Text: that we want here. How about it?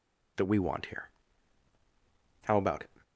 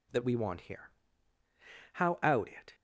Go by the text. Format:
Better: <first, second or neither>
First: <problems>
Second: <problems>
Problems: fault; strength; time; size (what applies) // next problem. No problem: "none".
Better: first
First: none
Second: says "out" for "about"; at 2.2 s